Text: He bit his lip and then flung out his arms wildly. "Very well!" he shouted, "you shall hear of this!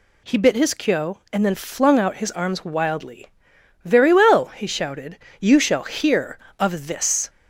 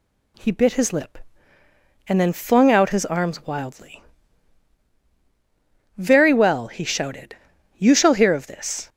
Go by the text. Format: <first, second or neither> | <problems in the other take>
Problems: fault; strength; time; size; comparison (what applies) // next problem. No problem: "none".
second | says "kyo" for "lip"; at 0.7 s